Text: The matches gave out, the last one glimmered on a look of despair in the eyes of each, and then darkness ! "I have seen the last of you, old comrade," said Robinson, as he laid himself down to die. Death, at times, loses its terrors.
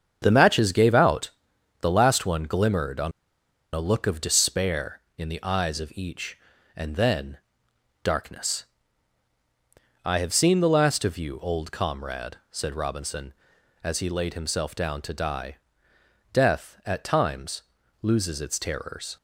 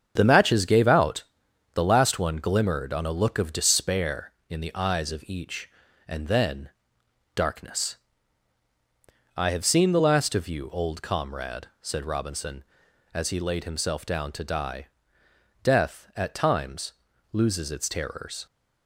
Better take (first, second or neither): second